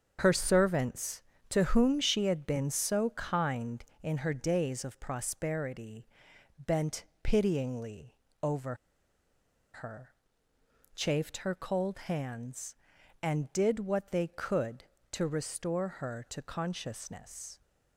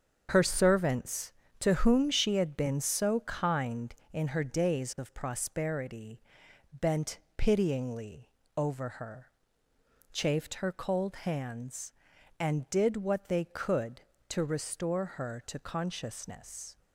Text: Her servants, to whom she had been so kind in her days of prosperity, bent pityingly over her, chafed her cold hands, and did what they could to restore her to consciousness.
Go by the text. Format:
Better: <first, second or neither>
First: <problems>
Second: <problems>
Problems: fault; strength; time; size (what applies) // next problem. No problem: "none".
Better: second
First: starts louder than the rest; strong; until 1.2 s; 7 dB // pauses between "bent" and "pityingly"; slight; at 7.0 s; 0.16 s long // pauses between "pityingly" and "over"; slight; at 8.1 s; 0.26 s long // pauses between "over" and "her"; at 8.7 s; 1.0 s long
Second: starts louder than the rest; strong; until 1.3 s; 7 dB // pauses between "bent" and "pityingly"; slight; at 7.1 s; 0.16 s long // pauses between "pityingly" and "over"; slight; at 8.2 s; 0.26 s long